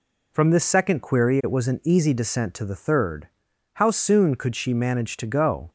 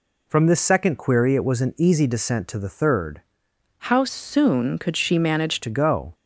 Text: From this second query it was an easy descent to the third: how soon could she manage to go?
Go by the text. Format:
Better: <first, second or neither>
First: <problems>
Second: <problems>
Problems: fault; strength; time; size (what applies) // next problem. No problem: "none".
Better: first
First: none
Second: changes voice from "how" to "manage"; from 3.7 to 5.6 s; 1.9 s long